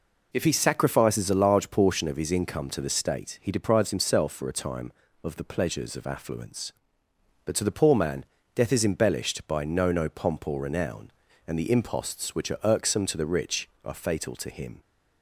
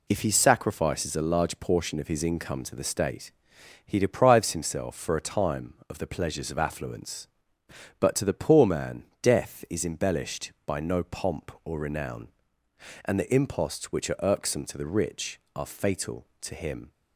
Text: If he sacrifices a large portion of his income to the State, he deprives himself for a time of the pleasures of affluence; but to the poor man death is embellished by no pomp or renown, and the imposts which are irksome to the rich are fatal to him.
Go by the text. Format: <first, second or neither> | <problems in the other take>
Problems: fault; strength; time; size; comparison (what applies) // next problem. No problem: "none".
second | pauses between "man" and "death"; slight; at 8.2 s; 0.30 s long; slight in the second // says "no" twice; at 9.9 s